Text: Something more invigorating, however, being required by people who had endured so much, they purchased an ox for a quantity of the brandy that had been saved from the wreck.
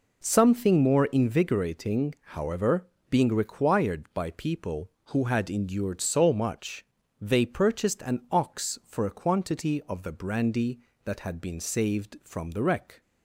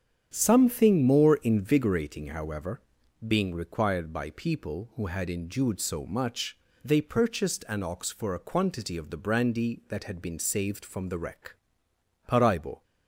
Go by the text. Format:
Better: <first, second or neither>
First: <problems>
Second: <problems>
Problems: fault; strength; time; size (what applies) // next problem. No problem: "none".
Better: first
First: none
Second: starts louder than the rest; strong; until 1.3 s; 9 dB // goes on to say "Paraibo"; from 12.2 s on; 0.56 s long